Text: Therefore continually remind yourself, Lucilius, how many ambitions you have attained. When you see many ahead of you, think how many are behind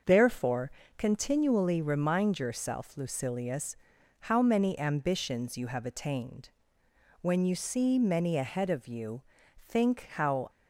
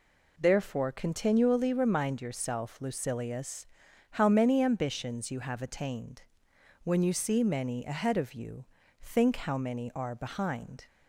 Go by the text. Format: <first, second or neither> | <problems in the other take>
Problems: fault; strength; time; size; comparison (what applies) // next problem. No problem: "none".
second | starts louder than the rest; until 1.3 s; 6 dB // pauses between "Therefore" and "continually"; slight; at 0.6 s; 0.28 s long // stops before "many are behind"; at 10.4 s